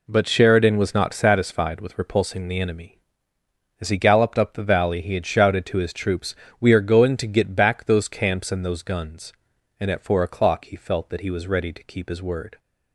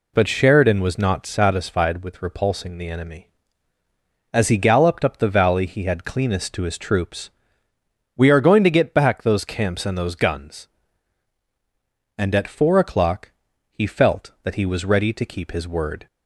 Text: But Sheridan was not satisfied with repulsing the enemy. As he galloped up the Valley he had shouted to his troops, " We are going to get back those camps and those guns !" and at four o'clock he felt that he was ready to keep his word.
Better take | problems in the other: first | says "cleanest" for "shouted"; at 6.0 s // pauses between "o'clock" and "he"; at 13.3 s; 0.40 s long

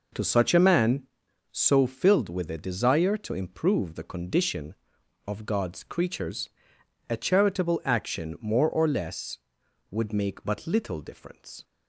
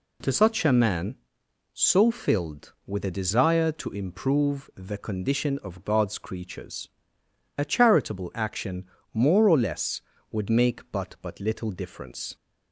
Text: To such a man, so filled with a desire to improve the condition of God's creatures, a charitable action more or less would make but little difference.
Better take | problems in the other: first | pauses between "action" and "more"; slight; at 8.8 s; 0.30 s long // says "but" twice; at 11.2 s

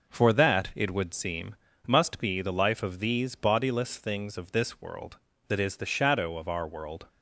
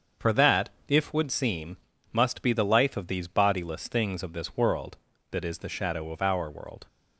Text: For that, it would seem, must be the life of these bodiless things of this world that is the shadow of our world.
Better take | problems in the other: first | starts louder than the rest; until 1.3 s; 7 dB // says "if" for "it"; at 0.8 s

